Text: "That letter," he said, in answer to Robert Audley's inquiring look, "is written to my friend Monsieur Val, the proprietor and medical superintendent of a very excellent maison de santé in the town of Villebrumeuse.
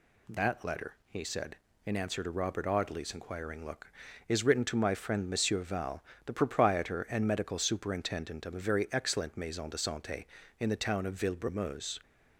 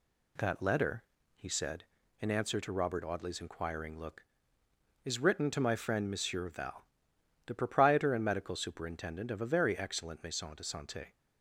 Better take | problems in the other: first | stops before "in the town of Villebrumeuse"; at 11.1 s

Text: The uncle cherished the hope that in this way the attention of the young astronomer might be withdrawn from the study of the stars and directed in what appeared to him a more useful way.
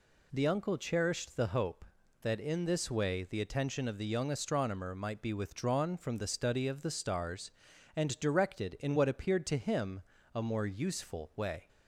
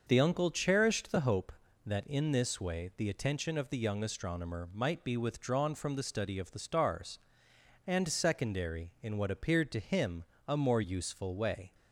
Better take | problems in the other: first | starts louder than the rest; until 1.0 s; 6 dB // says "secondary" for "directed"; at 8.0 s // pauses between "him" and "a"; slight; at 10.2 s; 0.24 s long; slight in the first

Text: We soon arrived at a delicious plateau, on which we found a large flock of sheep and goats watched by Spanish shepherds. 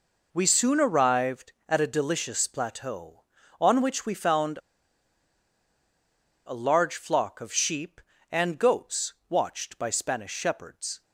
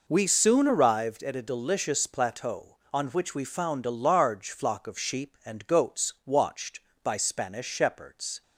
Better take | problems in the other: second | pauses between "found" and "a"; strong; at 4.6 s; 1.8 s long // pauses between "goats" and "watched"; slight; at 9.1 s; 0.16 s long

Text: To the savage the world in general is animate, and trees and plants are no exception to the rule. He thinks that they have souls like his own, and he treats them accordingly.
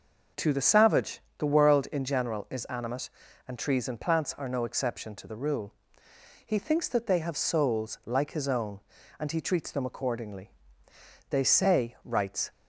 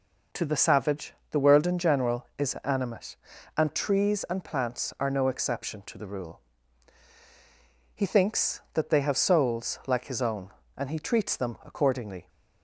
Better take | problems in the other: second | pauses between "savage" and "the"; slight; at 1.2 s; 0.18 s long; slight in the second // goes on to say "They say writes"; noticeable; from 11.3 s on; 1.2 s long

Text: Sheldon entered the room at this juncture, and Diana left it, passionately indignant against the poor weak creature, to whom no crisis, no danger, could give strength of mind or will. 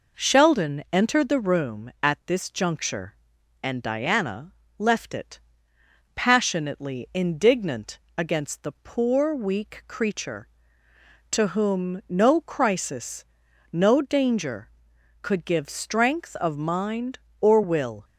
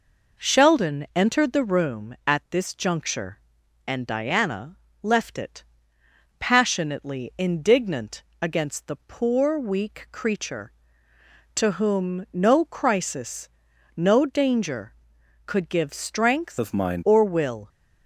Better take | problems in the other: first | pauses between "Diana" and "left"; slight; at 4.7 s; 0.26 s long; slight in the first // pauses between "indignant" and "against"; slight; at 8.2 s; 0.18 s long; slight in the first // changes voice from "of" to "mind"; from 16.5 to 17.0 s; 0.5 s long

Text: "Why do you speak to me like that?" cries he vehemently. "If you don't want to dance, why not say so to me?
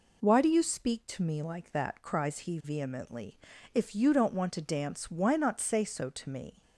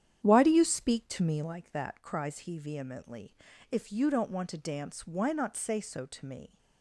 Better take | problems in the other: first | starts louder than the rest; strong; until 1.6 s; 9.5 dB

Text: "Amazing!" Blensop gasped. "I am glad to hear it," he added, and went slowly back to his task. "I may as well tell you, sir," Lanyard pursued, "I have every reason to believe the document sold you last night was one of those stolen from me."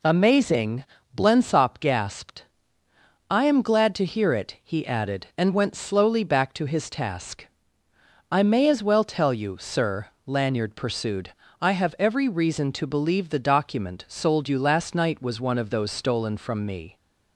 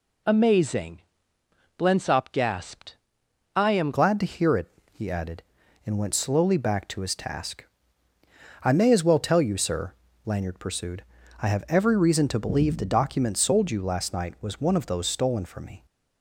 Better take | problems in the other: first | changes voice at "glad"; from 3.9 s on; 11.9 s long

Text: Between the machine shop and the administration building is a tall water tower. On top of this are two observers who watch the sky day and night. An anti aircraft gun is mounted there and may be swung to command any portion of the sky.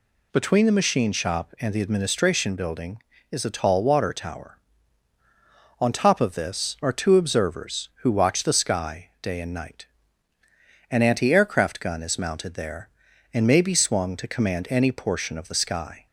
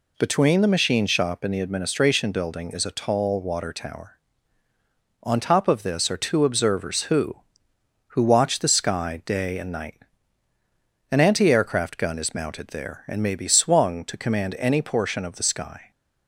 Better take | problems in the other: first | says "who" twice; at 8.0 s

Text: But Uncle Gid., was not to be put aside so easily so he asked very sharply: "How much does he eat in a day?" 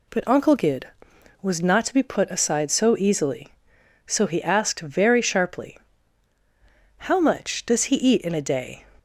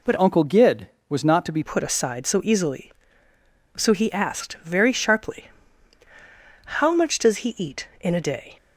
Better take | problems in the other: first | changes voice from "Uncle" to "be"; from 0.1 to 1.6 s; 1.5 s long

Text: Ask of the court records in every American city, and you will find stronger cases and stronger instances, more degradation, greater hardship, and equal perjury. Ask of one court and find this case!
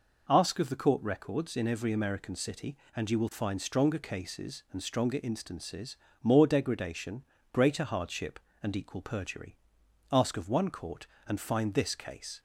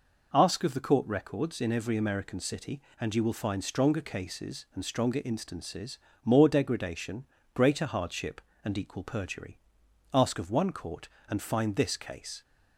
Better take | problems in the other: neither | none

